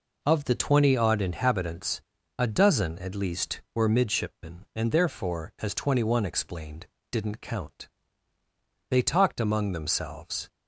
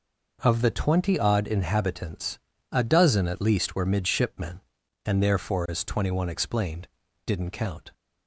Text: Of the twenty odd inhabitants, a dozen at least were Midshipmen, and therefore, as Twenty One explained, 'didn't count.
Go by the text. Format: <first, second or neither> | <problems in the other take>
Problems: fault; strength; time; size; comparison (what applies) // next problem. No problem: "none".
second | goes on to say "They talked among themselves"; from 8.9 s on; 1.5 s long